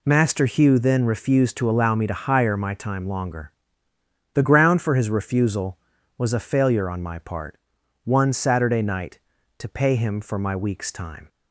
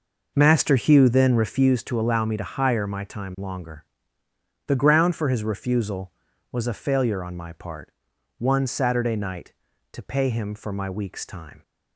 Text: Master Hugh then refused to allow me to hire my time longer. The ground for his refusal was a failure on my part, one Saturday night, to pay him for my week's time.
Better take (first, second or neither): first